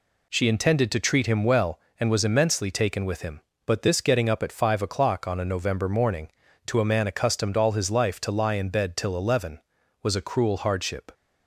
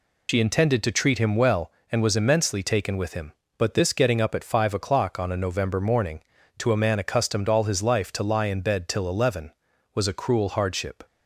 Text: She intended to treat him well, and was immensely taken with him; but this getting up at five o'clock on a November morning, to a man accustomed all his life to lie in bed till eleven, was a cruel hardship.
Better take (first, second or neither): first